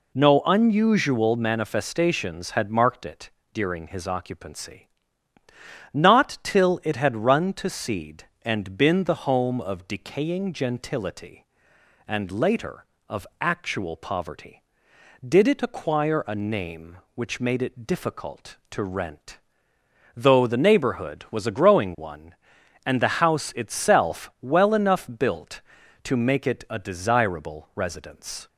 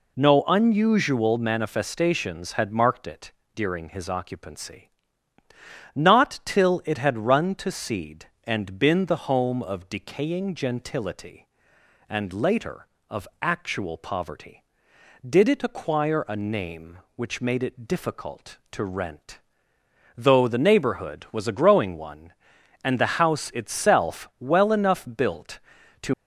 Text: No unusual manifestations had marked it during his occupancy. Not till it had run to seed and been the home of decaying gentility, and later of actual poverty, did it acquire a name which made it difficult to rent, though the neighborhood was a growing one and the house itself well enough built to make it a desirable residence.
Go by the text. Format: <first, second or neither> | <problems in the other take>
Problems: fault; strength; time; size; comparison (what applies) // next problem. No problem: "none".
first | pauses between "it" and "during"; slight; at 3.3 s; 0.20 s long; slight in the first // pauses between "of" and "actual"; slight; at 13.2 s; 0.16 s long; slight in the first // stops before "make it a desirable residence"; at 26.1 s